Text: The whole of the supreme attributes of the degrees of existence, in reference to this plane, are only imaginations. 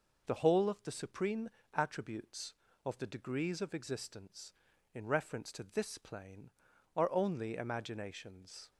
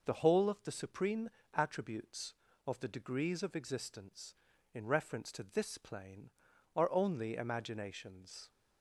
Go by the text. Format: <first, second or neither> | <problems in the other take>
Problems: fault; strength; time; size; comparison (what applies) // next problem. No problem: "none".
neither | pauses between "supreme" and "attributes"; slight; the same in both